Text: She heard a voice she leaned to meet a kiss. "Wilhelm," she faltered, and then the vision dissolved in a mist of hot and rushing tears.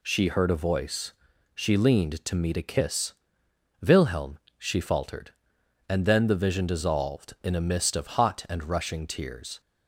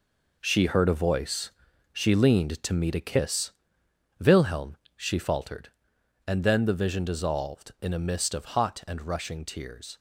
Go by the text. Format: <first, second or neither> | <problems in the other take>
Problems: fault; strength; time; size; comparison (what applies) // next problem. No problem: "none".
first | gets quieter; strong; throughout; 9 dB // pauses between "voice" and "she"; at 1.5 s; 0.42 s long; also in the first